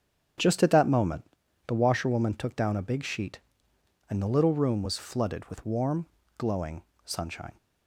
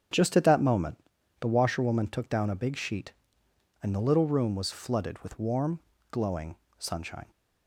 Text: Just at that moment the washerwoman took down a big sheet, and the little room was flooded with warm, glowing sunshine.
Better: neither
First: starts louder than the rest; strong; until 1.8 s; 8.5 dB // pauses between "moment" and "the"; at 1.2 s; 0.42 s long // pauses between "glowing" and "sunshine"; slight; at 6.8 s; 0.22 s long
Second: starts louder than the rest; strong; until 1.5 s; 8.5 dB // pauses between "moment" and "the"; at 0.9 s; 0.42 s long // pauses between "glowing" and "sunshine"; slight; at 6.5 s; 0.22 s long

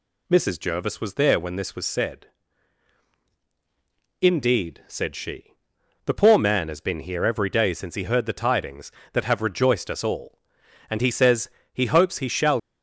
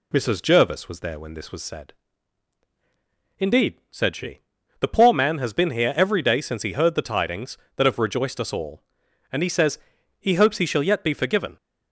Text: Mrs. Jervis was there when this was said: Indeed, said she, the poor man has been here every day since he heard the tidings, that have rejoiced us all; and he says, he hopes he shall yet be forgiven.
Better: second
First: stops before "yet be forgiven"; at 12.5 s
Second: none

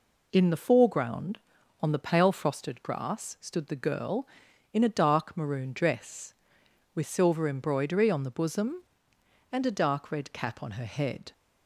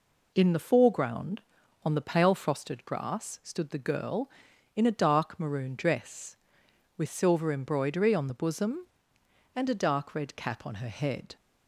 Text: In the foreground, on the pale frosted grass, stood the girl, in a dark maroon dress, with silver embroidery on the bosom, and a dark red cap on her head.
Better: neither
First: none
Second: none

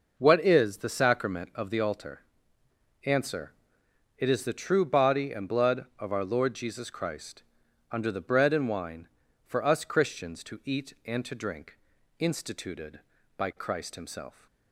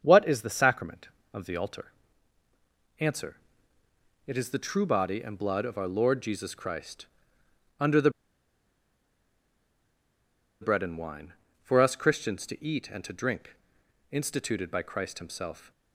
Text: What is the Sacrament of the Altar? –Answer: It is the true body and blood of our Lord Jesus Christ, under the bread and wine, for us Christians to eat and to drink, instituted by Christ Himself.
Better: first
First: none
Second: starts louder than the rest; strong; until 1.0 s; 7 dB // pauses between "the" and "bread"; strong; at 8.0 s; 2.5 s long

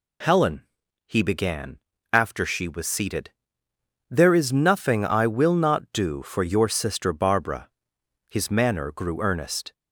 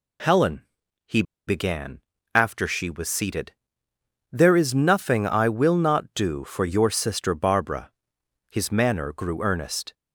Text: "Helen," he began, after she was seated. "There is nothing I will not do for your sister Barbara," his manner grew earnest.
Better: first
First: none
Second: pauses between "he" and "began"; slight; at 1.2 s; 0.24 s long

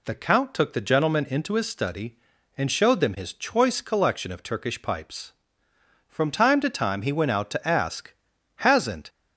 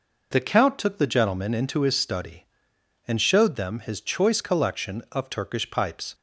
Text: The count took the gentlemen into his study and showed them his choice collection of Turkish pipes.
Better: second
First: goes on to say "From time to time he went out to ask Hasn't"; strong; from 6.0 s on; 3.0 s long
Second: none

